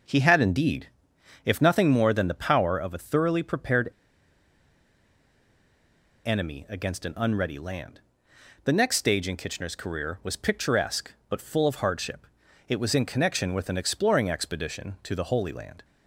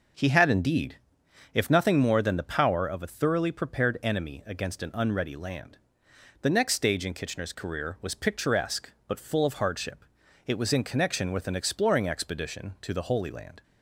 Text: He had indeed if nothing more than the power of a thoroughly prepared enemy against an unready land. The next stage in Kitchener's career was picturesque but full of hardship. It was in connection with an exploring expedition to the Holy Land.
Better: second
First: pauses between "indeed" and "if"; noticeable; at 0.8 s; 0.58 s long // pauses between "prepared" and "enemy"; strong; at 3.8 s; 2.3 s long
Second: pauses between "indeed" and "if"; noticeable; at 0.9 s; 0.58 s long

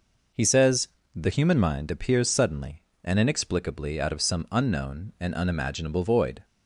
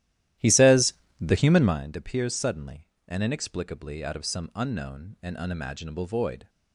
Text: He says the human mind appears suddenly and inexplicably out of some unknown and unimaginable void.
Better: first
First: pauses between "says" and "the"; slight; at 0.8 s; 0.26 s long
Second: starts louder than the rest; strong; until 1.8 s; 13.5 dB // pauses between "says" and "the"; slight; at 0.9 s; 0.26 s long

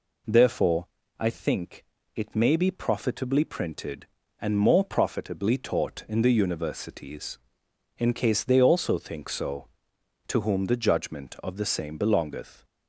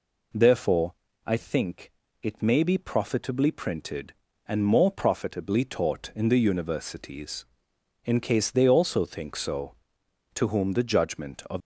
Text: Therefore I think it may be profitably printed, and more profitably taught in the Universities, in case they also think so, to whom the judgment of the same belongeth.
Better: first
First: pauses between "Therefore" and "I"; slight; at 0.8 s; 0.32 s long // pauses between "think" and "it"; slight; at 1.8 s; 0.30 s long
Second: pauses between "Therefore" and "I"; slight; at 0.9 s; 0.32 s long // pauses between "think" and "it"; slight; at 1.9 s; 0.30 s long // stops before "the same belongeth"; at 11.5 s

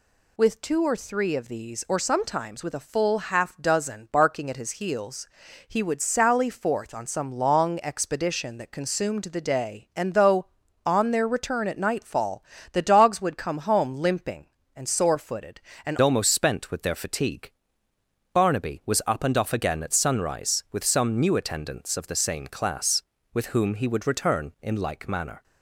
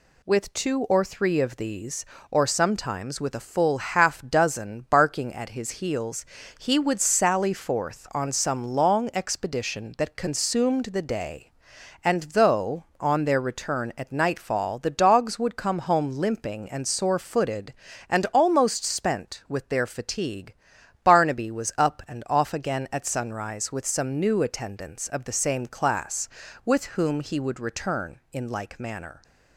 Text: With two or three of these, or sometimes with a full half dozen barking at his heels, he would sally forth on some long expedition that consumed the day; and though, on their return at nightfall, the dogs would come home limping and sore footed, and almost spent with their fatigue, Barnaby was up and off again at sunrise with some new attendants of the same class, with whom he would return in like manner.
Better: second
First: changes voice at "almost"; from 16.0 s on; 9.4 s long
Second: none

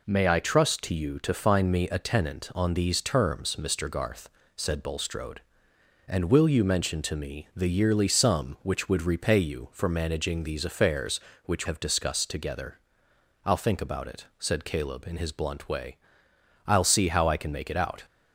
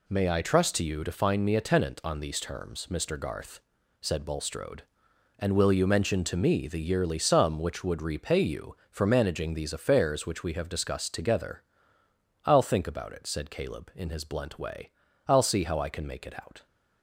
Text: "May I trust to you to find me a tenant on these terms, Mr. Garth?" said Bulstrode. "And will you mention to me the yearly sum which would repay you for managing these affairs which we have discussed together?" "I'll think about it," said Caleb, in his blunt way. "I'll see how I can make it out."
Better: second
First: skips "we"; at 11.6 s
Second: none

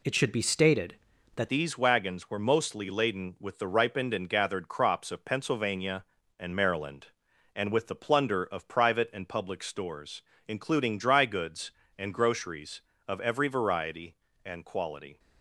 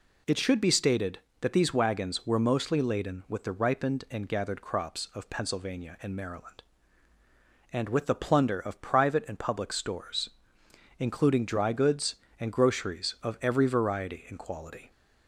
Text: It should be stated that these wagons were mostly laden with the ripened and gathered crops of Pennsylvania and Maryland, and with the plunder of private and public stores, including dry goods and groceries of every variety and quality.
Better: second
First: changes voice at "these"; from 1.4 s on; 13.7 s long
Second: none

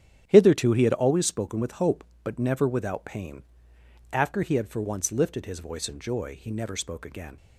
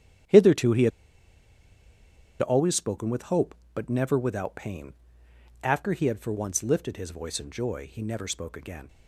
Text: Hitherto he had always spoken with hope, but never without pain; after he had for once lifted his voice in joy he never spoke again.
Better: first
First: starts louder than the rest; strong; until 1.2 s; 9 dB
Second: starts louder than the rest; strong; until 2.7 s; 9 dB // pauses between "had" and "always"; strong; at 0.9 s; 1.5 s long

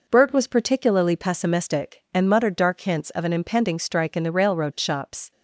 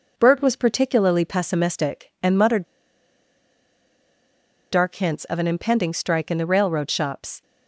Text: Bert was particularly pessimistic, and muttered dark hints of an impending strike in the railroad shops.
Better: first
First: none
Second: pauses between "muttered" and "dark"; strong; at 2.6 s; 2.0 s long

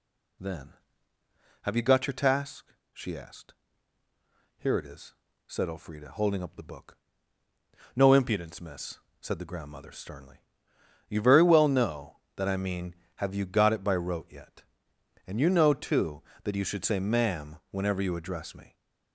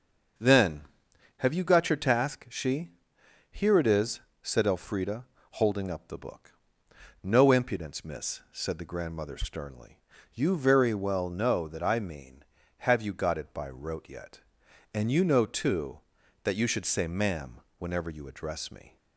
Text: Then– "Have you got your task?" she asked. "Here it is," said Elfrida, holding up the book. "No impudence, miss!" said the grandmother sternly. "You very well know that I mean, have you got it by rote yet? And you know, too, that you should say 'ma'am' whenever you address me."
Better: first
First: none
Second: starts louder than the rest; until 1.9 s; 6.5 dB // skips "asked"; at 3.1 s // pauses between "ma'am" and "whenever"; slight; at 17.6 s; 0.16 s long

